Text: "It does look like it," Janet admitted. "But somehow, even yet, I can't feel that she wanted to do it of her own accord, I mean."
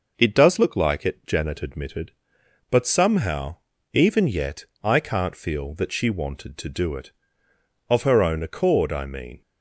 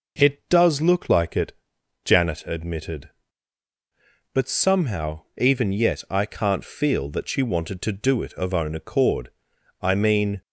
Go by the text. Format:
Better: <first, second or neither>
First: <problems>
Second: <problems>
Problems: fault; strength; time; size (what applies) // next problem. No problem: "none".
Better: first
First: none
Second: skips "her"; at 8.5 s